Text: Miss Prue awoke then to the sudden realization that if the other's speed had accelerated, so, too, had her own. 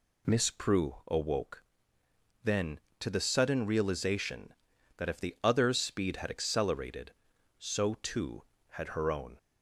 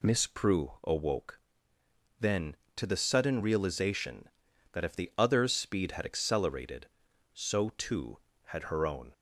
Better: neither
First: pauses between "awoke" and "then"; noticeable; at 1.6 s; 0.80 s long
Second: pauses between "awoke" and "then"; noticeable; at 1.3 s; 0.80 s long

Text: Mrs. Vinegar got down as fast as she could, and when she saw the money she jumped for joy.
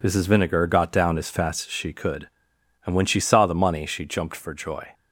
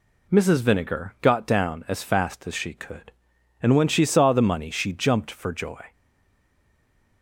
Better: first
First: none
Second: stays silent after the last word; noticeable; from 5.9 s on; 1.3 s long

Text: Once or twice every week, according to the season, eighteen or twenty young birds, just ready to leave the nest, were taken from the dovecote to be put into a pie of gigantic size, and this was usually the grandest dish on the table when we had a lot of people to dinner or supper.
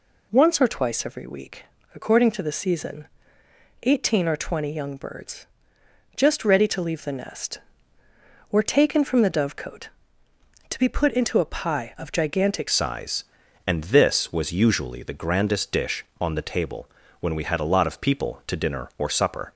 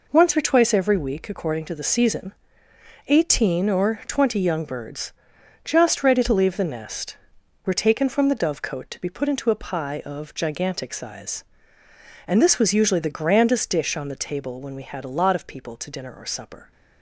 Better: second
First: changes voice at "size"; from 12.6 s on; 6.9 s long // pauses between "table" and "when"; slight; at 16.8 s; 0.30 s long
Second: none

